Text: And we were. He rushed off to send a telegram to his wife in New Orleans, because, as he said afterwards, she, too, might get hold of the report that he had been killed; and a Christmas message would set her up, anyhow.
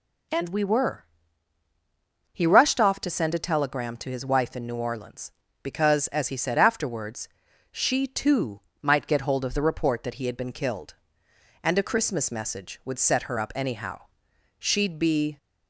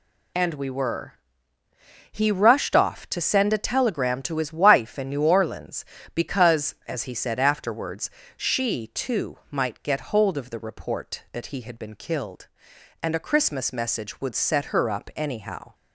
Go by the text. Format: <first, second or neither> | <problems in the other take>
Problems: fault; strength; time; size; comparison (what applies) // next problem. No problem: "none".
second | goes on to say "She'd be"; noticeable; from 14.5 s on; 0.78 s long